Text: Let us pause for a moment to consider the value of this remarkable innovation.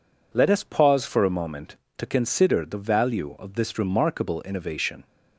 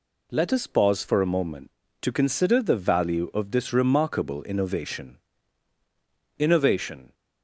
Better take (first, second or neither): first